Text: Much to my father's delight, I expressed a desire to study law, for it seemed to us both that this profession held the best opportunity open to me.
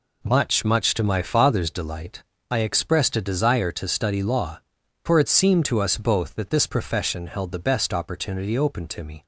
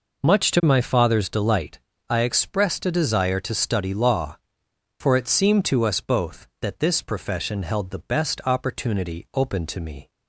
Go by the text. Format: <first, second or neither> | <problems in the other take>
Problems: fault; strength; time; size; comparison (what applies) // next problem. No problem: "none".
second | says "Much" twice; at 0.6 s